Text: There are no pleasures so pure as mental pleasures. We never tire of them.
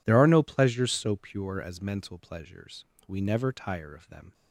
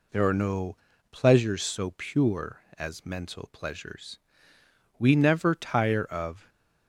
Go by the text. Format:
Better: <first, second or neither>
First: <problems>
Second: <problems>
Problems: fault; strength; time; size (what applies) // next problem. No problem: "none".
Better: first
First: none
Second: pauses between "no" and "pleasures"; slight; at 0.7 s; 0.36 s long // stops before "them"; at 6.4 s